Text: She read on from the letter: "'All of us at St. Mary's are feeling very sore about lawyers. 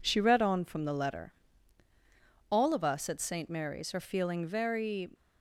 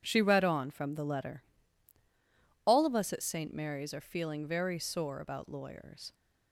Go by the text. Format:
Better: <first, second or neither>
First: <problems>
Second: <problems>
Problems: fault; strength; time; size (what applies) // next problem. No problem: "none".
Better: second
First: stops before "sore about lawyers"; at 5.1 s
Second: none